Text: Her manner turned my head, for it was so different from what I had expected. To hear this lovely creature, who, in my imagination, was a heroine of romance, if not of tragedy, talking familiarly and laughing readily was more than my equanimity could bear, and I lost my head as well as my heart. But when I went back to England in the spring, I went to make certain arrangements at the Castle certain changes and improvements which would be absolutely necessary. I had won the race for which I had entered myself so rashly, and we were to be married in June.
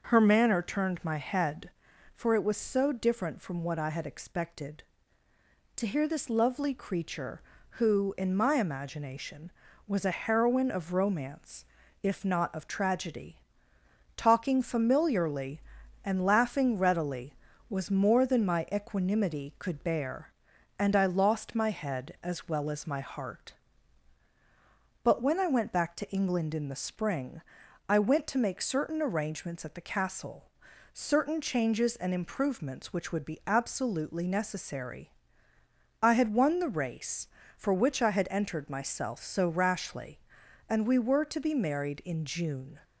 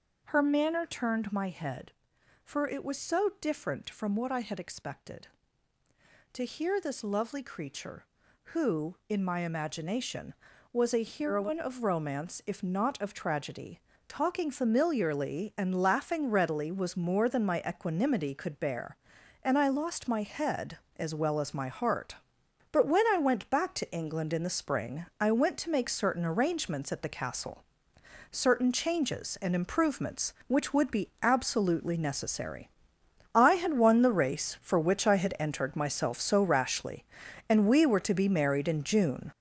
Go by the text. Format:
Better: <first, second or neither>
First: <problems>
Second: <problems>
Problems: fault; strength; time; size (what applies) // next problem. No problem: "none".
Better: first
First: pauses between "Castle" and "certain"; noticeable; at 30.4 s; 0.46 s long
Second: gets louder; throughout; 6.5 dB // pauses between "Castle" and "certain"; noticeable; at 27.6 s; 0.70 s long // pauses between "be" and "absolutely"; slight; at 31.0 s; 0.16 s long